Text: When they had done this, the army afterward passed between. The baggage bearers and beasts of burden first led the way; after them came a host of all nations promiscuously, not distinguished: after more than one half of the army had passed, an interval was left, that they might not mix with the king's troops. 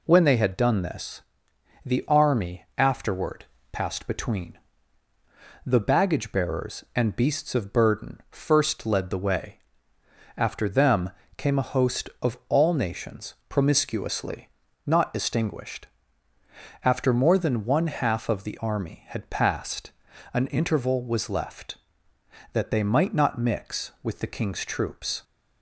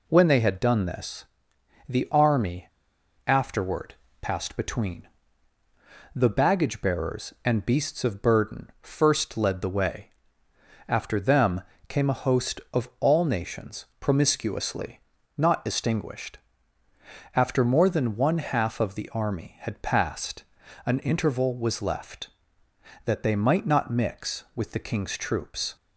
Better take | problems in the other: first | pauses between "army" and "afterward"; noticeable; at 2.6 s; 0.57 s long // pauses between "afterward" and "passed"; slight; at 3.9 s; 0.26 s long; slight in the first // pauses between "them" and "came"; slight; at 11.6 s; 0.26 s long; slight in the first // pauses between "nations" and "promiscuously"; slight; at 13.8 s; 0.16 s long; slight in the first

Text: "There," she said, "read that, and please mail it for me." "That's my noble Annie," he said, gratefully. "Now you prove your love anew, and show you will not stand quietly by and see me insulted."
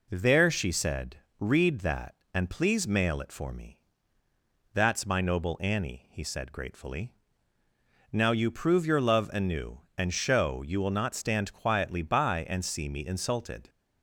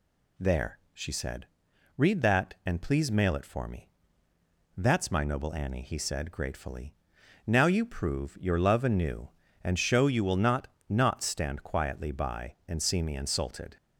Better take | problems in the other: first | says "not" twice; at 10.8 s

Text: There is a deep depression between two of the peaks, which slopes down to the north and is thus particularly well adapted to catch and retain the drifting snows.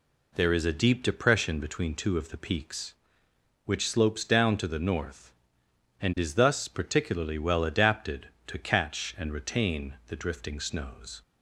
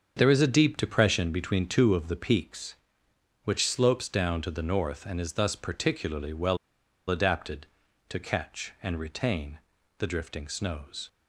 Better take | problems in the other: first | starts louder than the rest; until 1.1 s; 7 dB // pauses between "well" and "adapted"; noticeable; at 6.5 s; 0.52 s long // pauses between "retain" and "the"; at 9.5 s; 0.38 s long

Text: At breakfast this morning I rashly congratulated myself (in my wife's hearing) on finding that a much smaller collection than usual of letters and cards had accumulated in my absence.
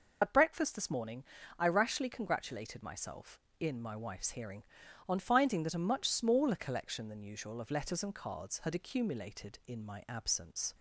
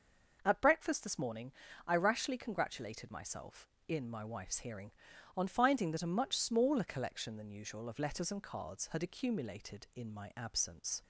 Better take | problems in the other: second | loses the start of "At"; at 0.2 s; 85 ms // pauses between "morning" and "I"; slight; at 1.2 s; 0.34 s long; slight in the second

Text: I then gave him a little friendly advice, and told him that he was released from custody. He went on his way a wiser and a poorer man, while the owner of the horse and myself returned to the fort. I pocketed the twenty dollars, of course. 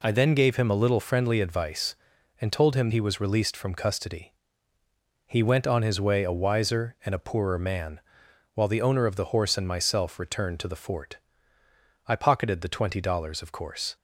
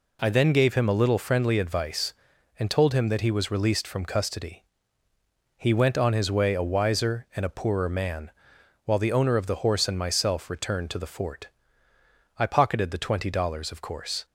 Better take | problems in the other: second | skips "that"; at 2.9 s

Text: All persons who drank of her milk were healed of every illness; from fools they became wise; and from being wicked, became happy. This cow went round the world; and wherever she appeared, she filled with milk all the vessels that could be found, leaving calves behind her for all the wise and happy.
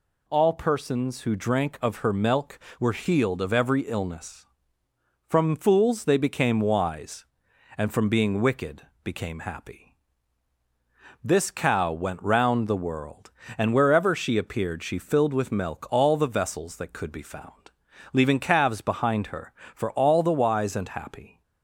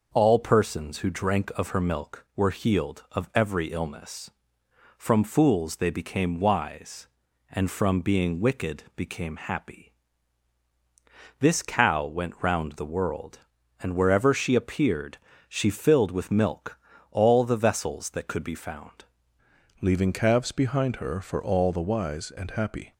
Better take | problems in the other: first | pauses between "milk" and "all"; slight; at 16.7 s; 0.32 s long // changes voice at "leaving"; from 19.8 s on; 3.1 s long

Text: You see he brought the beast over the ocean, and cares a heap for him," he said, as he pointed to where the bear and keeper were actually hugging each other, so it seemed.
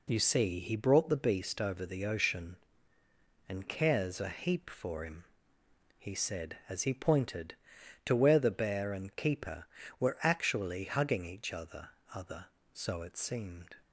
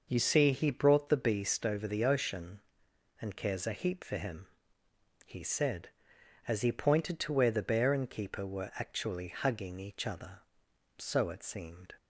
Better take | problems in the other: second | says "other" twice; at 12.1 s

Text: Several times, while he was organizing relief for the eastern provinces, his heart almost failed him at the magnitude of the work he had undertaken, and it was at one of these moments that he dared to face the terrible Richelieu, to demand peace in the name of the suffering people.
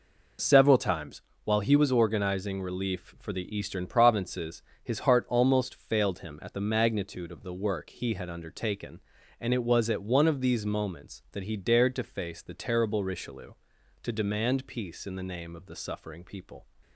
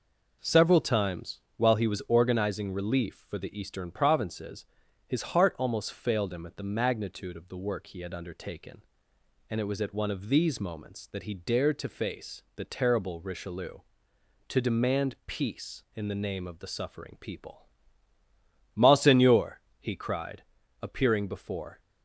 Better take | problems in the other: first | goes on to say "Monseigneur he cried appearing before"; strong; from 18.7 s on; 3.0 s long

